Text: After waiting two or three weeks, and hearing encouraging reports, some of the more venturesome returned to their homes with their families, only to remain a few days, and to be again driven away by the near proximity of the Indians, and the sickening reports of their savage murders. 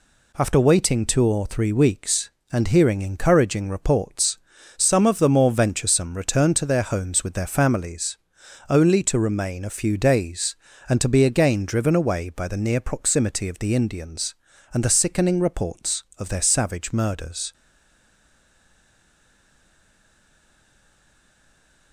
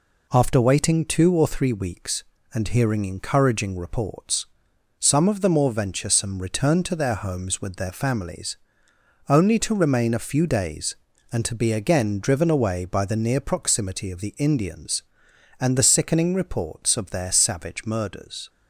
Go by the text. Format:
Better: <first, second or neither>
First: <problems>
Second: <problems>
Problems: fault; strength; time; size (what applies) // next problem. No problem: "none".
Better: second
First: stays silent after the last word; strong; from 17.5 s on; 4.4 s long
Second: none